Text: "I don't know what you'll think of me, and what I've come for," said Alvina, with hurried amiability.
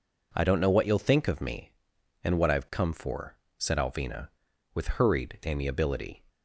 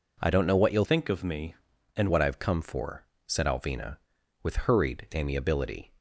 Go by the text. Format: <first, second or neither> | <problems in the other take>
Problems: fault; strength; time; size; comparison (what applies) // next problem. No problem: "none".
first | changes voice from "think" to "and"; from 0.8 to 2.1 s; 1.3 s long